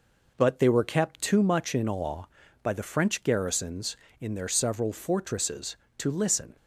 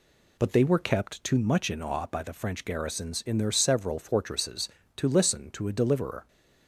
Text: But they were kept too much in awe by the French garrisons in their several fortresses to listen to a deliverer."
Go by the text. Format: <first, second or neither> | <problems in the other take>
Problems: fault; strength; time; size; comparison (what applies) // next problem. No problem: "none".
second | stops before "to a deliverer"; at 6.5 s